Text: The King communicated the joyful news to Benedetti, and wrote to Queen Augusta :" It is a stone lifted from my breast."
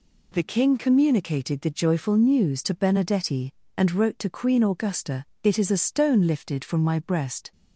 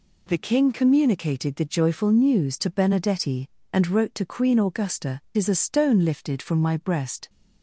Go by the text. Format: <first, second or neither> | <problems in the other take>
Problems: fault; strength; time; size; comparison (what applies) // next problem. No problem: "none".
first | skips "It"; at 5.3 s